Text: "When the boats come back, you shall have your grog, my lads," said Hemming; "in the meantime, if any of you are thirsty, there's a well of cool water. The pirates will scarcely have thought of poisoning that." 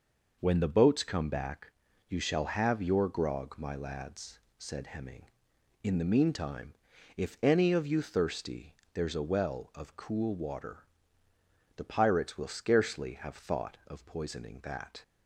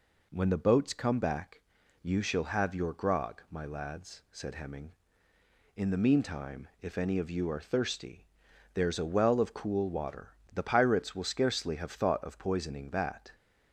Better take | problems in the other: second | skips "are"; at 8.0 s

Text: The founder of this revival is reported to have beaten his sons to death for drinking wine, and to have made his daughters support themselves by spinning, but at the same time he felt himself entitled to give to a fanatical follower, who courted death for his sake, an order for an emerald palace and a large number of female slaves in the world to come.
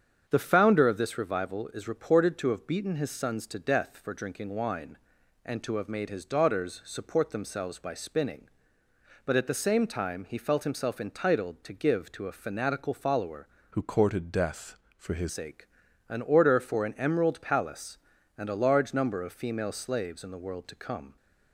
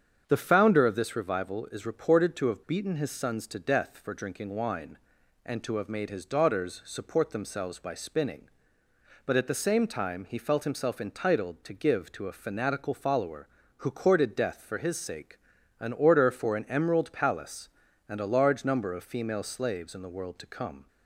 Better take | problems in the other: second | starts louder than the rest; strong; until 1.2 s; 8 dB; strong in the second // changes voice from "who" to "his"; from 13.7 to 15.2 s; 1.5 s long

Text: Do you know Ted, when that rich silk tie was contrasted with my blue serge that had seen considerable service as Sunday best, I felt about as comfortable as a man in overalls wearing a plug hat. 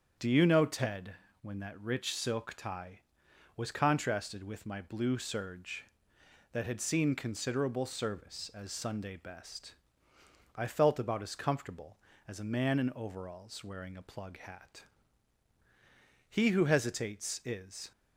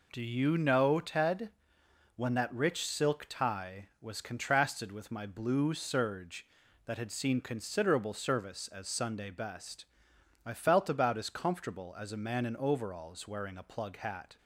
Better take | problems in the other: second | starts louder than the rest; strong; until 1.5 s; 7.5 dB // goes on to say "He who hesitates is"; from 16.2 s on; 1.6 s long

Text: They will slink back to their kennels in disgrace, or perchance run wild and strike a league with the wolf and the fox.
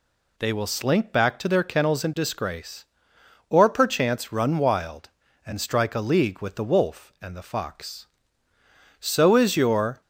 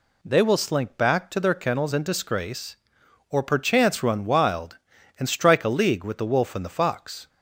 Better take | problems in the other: second | goes on to say "So is your"; noticeable; from 9.0 s on; 1.0 s long

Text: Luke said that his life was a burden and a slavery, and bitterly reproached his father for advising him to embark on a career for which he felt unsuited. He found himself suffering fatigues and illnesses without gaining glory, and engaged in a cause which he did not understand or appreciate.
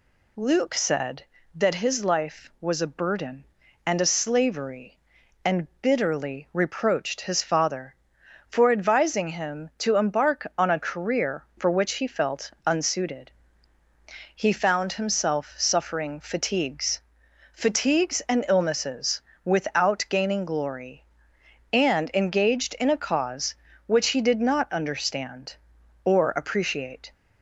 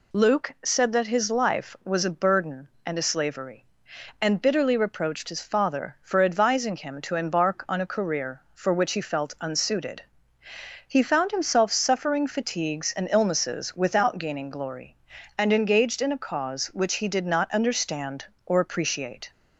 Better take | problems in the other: second | pauses between "and" and "bitterly"; slight; at 5.6 s; 0.16 s long // says "fatigues" twice; at 17.5 s // pauses between "illnesses" and "without"; slight; at 19.2 s; 0.24 s long

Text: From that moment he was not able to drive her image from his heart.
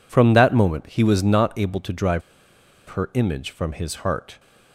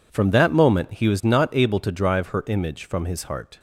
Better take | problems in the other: second | pauses between "drive" and "her"; noticeable; at 2.2 s; 0.68 s long

